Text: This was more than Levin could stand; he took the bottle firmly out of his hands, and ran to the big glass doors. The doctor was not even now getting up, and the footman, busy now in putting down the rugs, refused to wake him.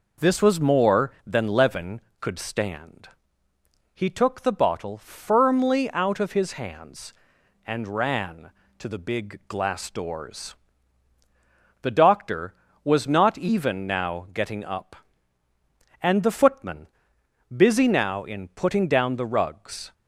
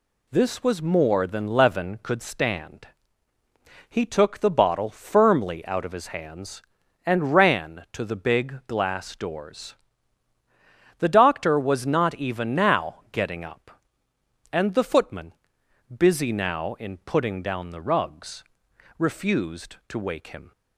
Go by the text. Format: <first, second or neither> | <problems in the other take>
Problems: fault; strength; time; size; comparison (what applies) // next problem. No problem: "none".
second | stops before "refused to wake him"; at 19.9 s